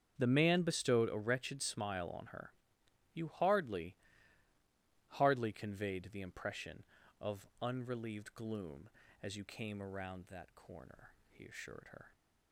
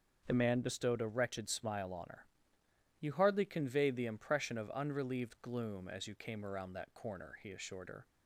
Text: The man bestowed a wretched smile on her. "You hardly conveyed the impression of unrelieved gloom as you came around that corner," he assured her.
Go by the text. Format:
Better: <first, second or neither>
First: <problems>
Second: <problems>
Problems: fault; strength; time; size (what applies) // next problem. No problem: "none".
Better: second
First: starts louder than the rest; strong; until 1.2 s; 7.5 dB // says "hardly" twice; at 5.0 s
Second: starts louder than the rest; until 1.2 s; 6.5 dB